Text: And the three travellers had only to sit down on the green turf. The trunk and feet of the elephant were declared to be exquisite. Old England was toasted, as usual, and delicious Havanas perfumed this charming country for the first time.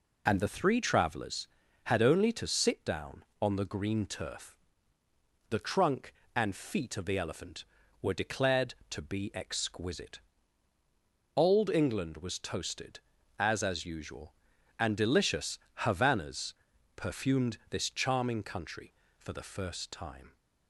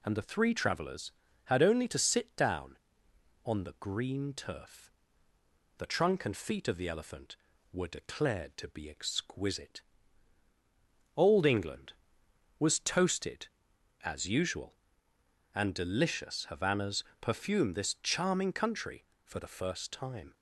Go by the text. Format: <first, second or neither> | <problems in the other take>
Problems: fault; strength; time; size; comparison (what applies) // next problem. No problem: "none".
second | says "as" twice; at 13.6 s // pauses between "delicious" and "Havanas"; slight; at 15.5 s; 0.24 s long // pauses between "Havanas" and "perfumed"; at 16.5 s; 0.42 s long; slight in the second